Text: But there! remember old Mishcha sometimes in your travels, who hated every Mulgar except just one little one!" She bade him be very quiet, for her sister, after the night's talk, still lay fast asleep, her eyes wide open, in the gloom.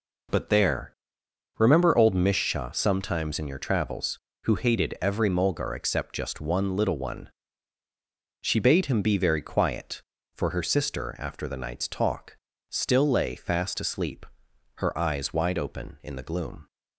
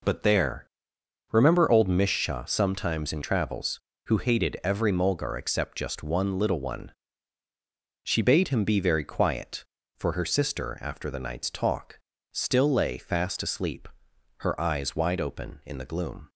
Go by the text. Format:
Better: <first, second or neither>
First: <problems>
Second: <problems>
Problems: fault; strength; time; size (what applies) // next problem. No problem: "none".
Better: first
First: none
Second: skips "your"; at 3.2 s